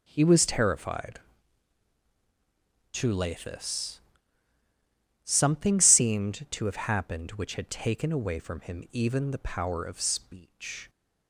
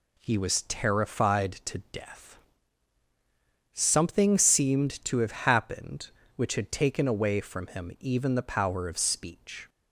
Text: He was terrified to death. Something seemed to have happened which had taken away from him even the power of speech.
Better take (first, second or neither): second